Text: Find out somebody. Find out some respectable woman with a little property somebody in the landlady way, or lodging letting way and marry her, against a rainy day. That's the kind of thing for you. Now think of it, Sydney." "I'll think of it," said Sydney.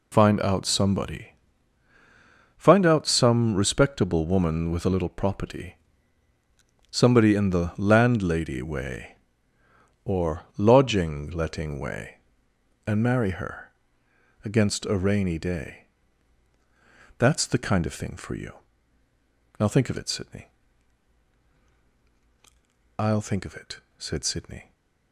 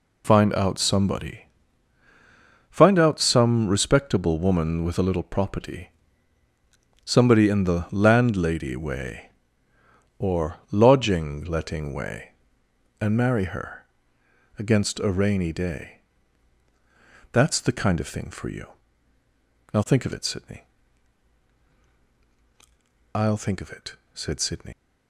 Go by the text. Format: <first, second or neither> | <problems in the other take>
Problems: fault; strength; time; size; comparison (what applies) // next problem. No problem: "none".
first | pauses between "property" and "somebody"; at 5.8 s; 1.1 s long; also in the first // pauses between "or" and "lodging"; slight; at 10.5 s; 0.16 s long; slight in the first // leaves "Sydney" unfinished; at 24.7 s; 150 ms